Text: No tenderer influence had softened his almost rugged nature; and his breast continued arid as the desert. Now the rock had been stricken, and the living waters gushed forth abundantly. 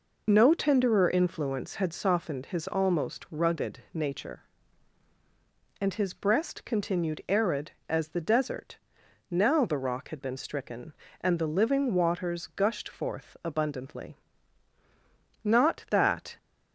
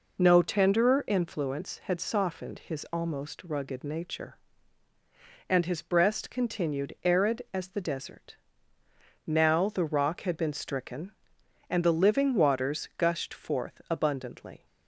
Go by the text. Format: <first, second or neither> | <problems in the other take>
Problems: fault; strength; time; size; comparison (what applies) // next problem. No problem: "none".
second | pauses between "rugged" and "nature"; slight; at 3.7 s; 0.16 s long // goes on to say "Not that"; noticeable; from 15.4 s on; 0.94 s long